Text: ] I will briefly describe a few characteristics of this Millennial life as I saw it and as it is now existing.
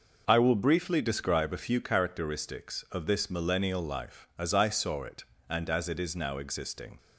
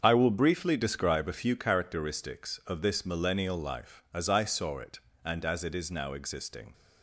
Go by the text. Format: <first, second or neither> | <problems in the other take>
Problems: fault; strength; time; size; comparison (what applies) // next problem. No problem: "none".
first | gets quieter; strong; throughout; 10.5 dB